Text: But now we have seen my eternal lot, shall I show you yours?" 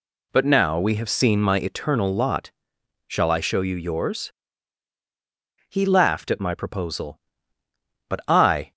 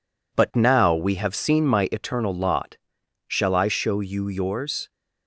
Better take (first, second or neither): second